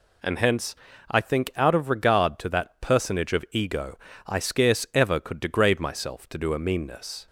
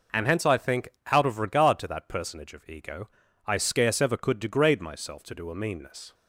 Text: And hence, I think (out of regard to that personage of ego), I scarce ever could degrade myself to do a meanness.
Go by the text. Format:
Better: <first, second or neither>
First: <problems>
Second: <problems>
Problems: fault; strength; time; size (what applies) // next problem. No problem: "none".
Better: neither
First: none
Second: none